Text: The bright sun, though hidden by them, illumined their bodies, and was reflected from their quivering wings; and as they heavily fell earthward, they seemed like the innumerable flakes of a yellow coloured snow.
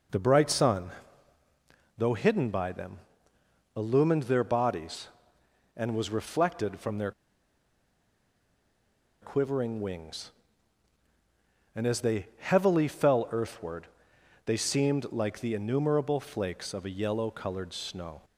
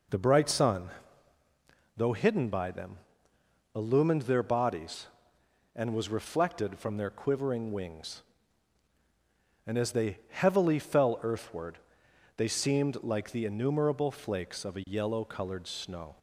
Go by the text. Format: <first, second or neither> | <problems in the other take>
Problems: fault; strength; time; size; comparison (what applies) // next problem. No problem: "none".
second | pauses between "their" and "quivering"; strong; at 7.1 s; 2.0 s long